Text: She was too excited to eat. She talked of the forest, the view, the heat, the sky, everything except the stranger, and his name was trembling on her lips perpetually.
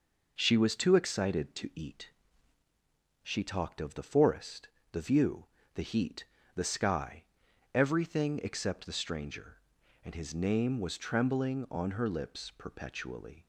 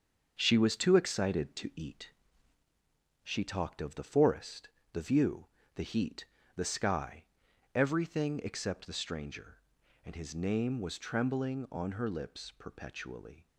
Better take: first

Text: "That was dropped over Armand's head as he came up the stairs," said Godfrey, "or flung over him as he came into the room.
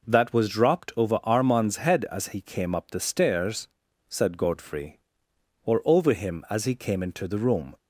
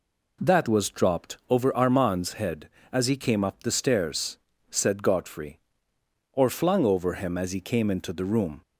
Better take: second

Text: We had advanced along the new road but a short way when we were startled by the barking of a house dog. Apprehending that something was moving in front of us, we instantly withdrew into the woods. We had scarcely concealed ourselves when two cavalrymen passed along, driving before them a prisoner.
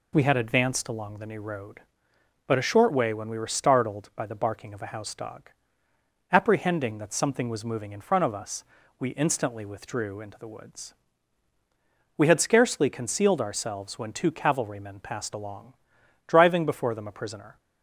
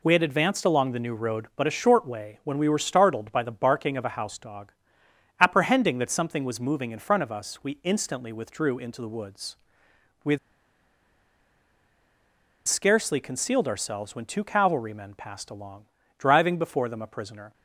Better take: first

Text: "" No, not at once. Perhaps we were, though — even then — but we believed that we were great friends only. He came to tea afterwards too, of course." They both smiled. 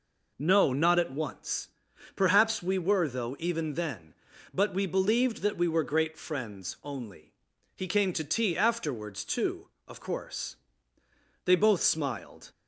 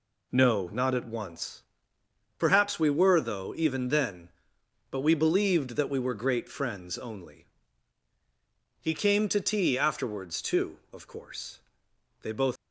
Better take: first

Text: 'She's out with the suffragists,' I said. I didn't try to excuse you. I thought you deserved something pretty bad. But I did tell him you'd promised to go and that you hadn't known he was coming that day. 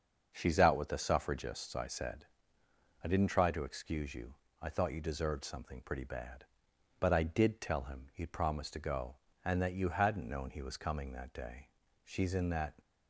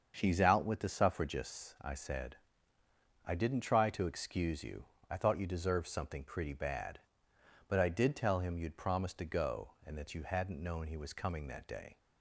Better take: second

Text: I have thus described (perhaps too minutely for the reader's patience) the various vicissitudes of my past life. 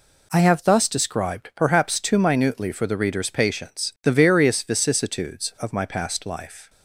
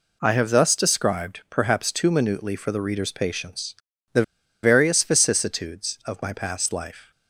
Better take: first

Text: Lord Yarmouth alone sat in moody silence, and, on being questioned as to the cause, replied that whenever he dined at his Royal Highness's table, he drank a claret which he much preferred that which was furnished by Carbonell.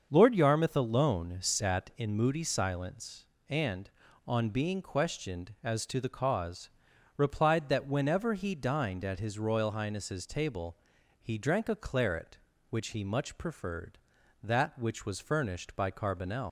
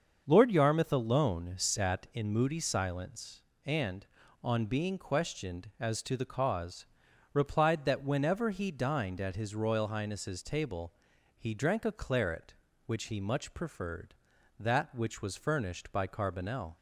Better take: second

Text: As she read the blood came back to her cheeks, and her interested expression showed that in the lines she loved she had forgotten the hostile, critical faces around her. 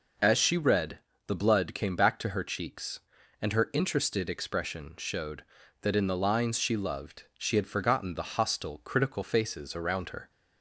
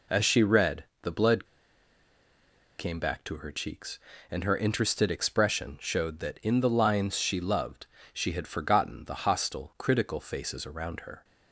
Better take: first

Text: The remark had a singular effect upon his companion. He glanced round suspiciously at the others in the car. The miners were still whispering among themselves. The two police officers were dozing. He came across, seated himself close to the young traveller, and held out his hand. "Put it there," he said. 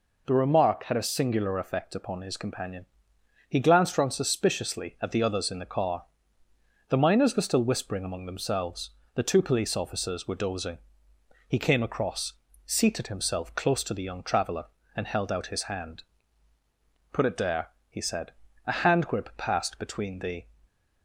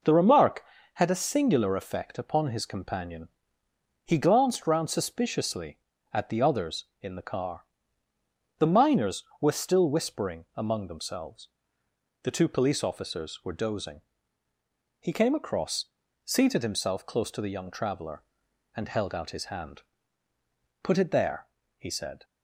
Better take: second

